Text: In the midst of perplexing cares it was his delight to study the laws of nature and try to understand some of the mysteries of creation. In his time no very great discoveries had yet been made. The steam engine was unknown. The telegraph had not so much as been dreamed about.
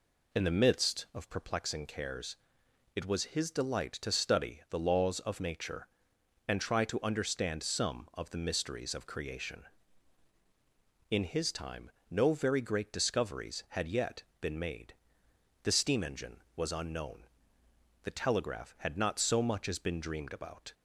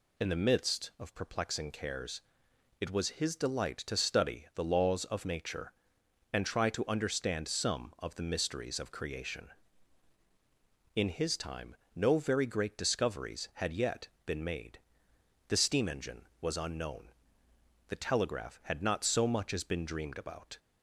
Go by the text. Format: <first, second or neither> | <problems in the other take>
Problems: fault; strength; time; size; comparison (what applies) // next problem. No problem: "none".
second | starts louder than the rest; slight; until 1.6 s; 2.5 dB // pauses between "cares" and "it"; noticeable; at 2.3 s; 0.58 s long; noticeable in the second // pauses between "time" and "no"; slight; at 11.9 s; 0.18 s long; slight in the second // pauses between "yet" and "been"; slight; at 14.2 s; 0.16 s long; slight in the second